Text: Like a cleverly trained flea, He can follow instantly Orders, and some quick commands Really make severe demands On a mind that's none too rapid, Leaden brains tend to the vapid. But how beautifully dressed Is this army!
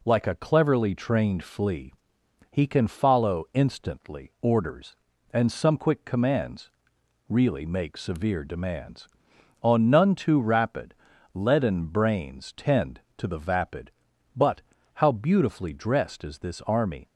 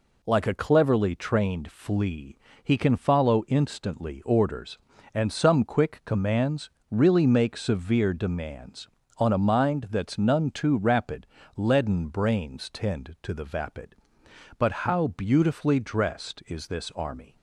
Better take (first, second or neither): second